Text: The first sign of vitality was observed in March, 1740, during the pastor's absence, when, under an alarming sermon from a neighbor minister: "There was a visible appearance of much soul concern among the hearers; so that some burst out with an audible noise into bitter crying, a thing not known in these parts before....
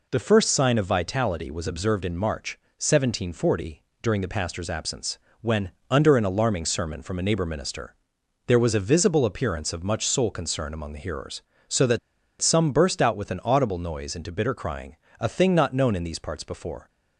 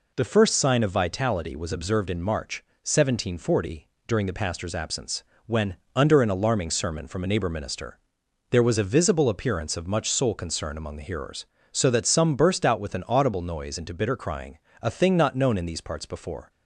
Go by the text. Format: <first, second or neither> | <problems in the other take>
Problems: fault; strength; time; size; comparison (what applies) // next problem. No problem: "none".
second | pauses between "that" and "some"; at 11.9 s; 0.42 s long